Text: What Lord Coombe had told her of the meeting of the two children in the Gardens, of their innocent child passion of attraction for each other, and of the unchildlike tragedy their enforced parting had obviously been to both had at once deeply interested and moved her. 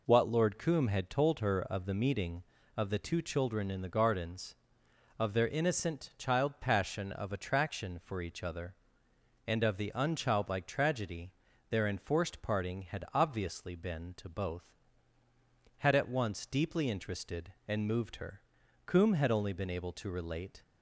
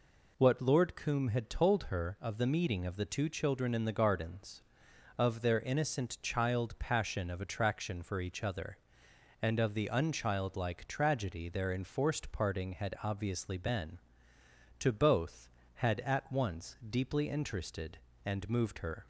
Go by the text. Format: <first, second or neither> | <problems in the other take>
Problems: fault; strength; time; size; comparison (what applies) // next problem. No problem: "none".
second | pauses between "tragedy" and "their"; at 11.3 s; 0.38 s long // goes on to say "Coombe had only been able to relate"; strong; from 18.8 s on; 1.7 s long